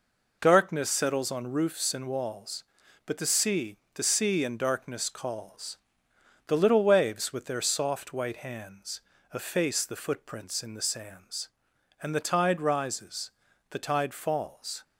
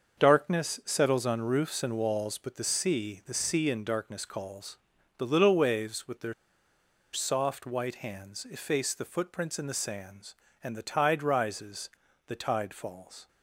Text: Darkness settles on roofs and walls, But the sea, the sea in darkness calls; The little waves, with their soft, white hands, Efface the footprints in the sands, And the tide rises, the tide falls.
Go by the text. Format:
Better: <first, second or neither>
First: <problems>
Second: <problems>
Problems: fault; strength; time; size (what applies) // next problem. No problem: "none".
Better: first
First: none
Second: starts louder than the rest; until 1.2 s; 6.5 dB // pauses between "their" and "soft"; noticeable; at 6.3 s; 0.79 s long